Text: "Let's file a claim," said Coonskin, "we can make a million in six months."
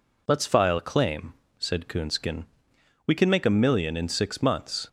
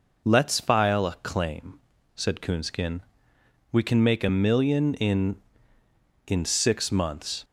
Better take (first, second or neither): first